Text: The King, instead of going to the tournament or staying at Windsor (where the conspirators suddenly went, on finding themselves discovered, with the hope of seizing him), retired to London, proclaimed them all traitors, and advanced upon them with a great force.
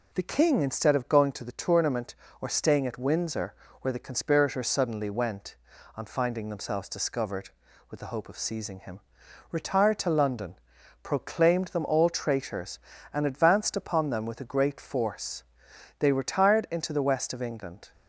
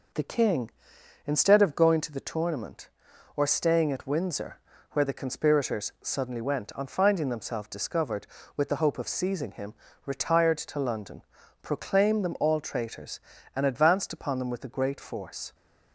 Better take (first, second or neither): second